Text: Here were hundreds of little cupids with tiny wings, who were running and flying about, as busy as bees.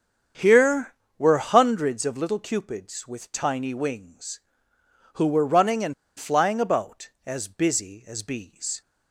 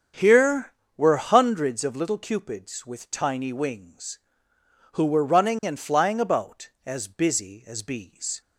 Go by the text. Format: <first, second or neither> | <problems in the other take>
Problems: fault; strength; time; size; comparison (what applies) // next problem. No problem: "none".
second | starts louder than the rest; strong; until 1.6 s; 7.5 dB; strong in the second // pauses between "and" and "flying"; slight; at 5.9 s; 0.24 s long